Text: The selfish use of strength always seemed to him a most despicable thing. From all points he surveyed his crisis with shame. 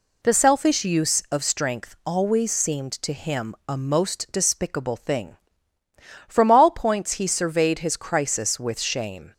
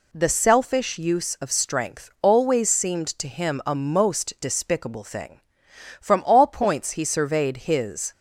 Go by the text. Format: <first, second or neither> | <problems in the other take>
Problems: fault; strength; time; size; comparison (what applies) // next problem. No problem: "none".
first | stops before "crisis with shame"; at 8.1 s